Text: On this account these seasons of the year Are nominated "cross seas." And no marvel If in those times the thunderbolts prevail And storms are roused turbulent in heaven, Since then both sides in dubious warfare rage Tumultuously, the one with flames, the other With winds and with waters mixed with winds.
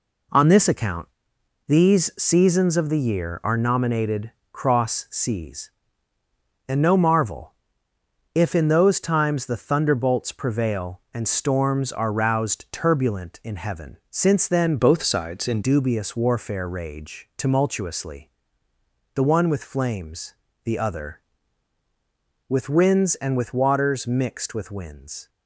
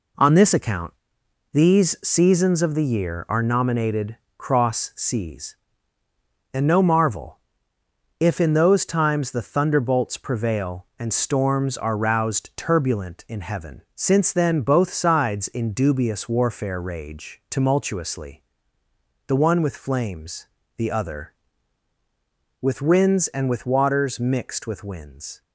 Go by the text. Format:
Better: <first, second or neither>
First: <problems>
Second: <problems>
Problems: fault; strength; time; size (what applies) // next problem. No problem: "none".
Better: second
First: pauses between "account" and "these"; noticeable; at 1.0 s; 0.60 s long // pauses between "nominated" and "cross"; slight; at 4.3 s; 0.22 s long // pauses between "marvel" and "If"; noticeable; at 7.5 s; 0.80 s long // changes voice from "both" to "in"; from 14.7 to 15.6 s; 0.9 s long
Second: pauses between "account" and "these"; noticeable; at 0.9 s; 0.60 s long // pauses between "nominated" and "cross"; slight; at 4.1 s; 0.22 s long // pauses between "marvel" and "If"; noticeable; at 7.4 s; 0.80 s long